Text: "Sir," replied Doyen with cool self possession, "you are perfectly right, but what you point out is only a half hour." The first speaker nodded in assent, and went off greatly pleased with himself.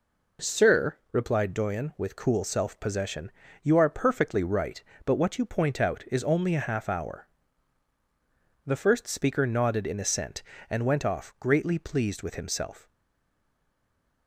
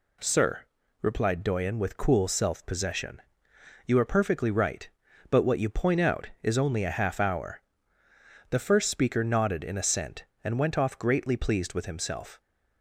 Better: second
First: stays silent after the last word; noticeable; from 12.8 s on; 1.4 s long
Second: none

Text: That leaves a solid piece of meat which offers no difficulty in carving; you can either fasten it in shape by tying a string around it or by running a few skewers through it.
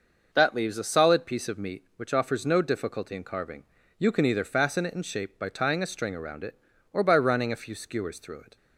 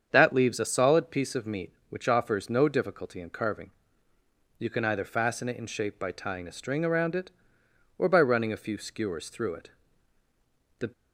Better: first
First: none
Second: starts louder than the rest; strong; until 1.1 s; 7.5 dB // goes on to say "The"; slight; from 10.7 s on; 0.14 s long

